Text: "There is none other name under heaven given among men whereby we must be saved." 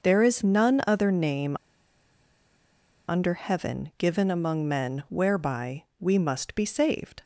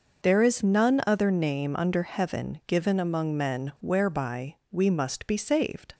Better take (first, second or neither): second